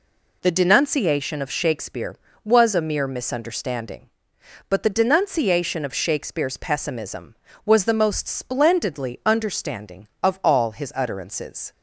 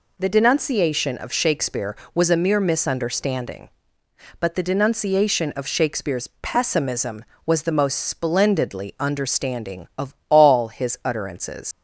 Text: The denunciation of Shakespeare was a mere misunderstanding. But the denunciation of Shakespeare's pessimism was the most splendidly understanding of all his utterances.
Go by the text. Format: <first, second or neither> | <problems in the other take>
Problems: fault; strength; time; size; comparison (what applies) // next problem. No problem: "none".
first | leaves "utterances" unfinished; at 11.7 s; 115 ms